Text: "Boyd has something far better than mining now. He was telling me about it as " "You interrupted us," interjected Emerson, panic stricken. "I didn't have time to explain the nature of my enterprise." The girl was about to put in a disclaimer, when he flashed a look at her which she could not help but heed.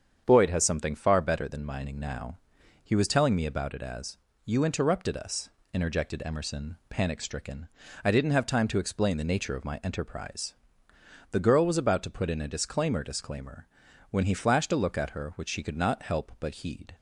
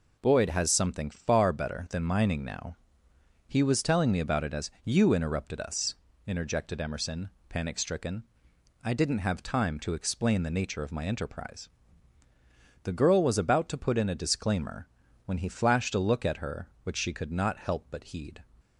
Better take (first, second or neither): second